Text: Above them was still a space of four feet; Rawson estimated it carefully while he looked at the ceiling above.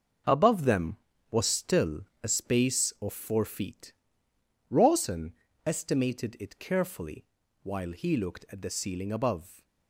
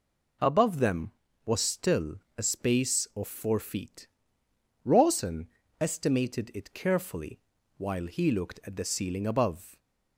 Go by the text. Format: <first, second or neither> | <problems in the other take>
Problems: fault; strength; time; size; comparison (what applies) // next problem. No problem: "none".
second | gets quieter; strong; throughout; 9.5 dB // pauses between "still" and "a"; slight; at 2.0 s; 0.18 s long; slight in the second // pauses between "Rawson" and "estimated"; slight; at 5.3 s; 0.34 s long; slight in the second // pauses between "carefully" and "while"; at 7.2 s; 0.40 s long; also in the second